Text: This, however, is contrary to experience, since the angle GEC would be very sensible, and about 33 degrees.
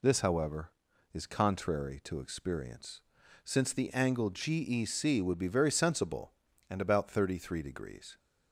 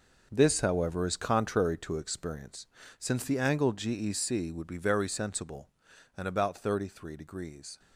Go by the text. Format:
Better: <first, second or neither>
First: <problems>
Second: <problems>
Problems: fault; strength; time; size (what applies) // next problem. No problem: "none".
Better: first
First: none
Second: gets quieter; strong; throughout; 11 dB